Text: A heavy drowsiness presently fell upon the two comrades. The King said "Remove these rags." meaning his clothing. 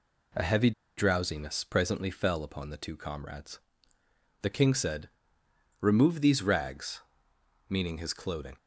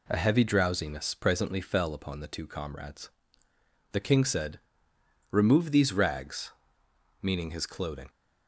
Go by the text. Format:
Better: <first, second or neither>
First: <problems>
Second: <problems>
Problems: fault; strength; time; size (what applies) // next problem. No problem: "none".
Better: second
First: pauses between "heavy" and "drowsiness"; slight; at 0.7 s; 0.26 s long // pauses between "said" and "Remove"; noticeable; at 5.1 s; 0.70 s long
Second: pauses between "said" and "Remove"; noticeable; at 4.6 s; 0.70 s long